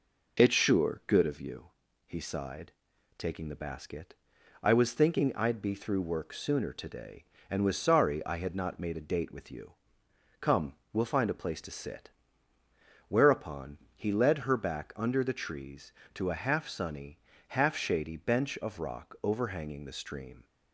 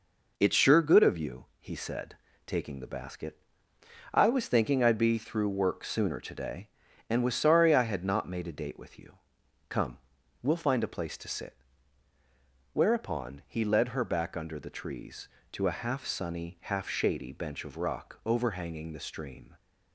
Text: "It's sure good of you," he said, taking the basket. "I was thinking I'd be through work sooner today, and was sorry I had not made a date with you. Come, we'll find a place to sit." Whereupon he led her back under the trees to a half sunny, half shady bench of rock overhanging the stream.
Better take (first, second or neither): second